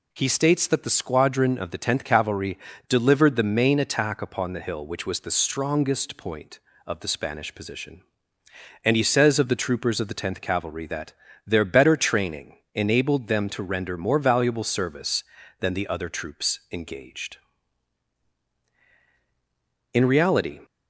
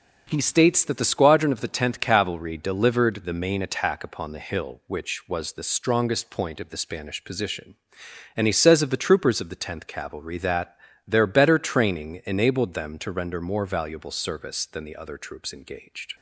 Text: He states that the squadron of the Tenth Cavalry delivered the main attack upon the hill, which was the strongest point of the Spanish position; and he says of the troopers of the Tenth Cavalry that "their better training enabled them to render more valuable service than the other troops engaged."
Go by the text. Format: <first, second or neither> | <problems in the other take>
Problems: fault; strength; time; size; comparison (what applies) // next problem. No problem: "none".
second | pauses between "Cavalry" and "delivered"; slight; at 2.5 s; 0.30 s long // pauses between "that" and "their"; slight; at 11.1 s; 0.34 s long; slight in the second // pauses between "training" and "enabled"; slight; at 12.5 s; 0.18 s long // goes on to say "In reality"; noticeable; from 19.9 s on; 0.66 s long